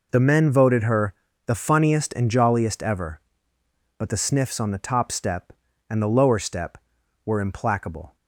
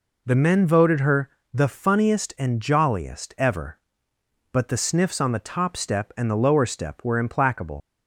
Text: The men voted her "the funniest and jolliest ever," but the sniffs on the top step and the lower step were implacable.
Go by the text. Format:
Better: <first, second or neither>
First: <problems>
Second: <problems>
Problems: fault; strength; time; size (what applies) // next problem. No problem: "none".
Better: first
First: pauses between "her" and "the"; slight; at 1.1 s; 0.32 s long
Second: pauses between "her" and "the"; slight; at 1.2 s; 0.24 s long // leaves "implacable" unfinished; at 7.8 s; 80 ms